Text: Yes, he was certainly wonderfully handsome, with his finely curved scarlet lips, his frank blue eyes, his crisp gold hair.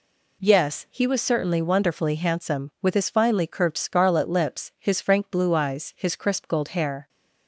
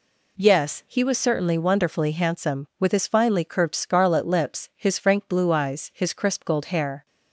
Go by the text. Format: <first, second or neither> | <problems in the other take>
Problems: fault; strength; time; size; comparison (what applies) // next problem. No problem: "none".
neither | none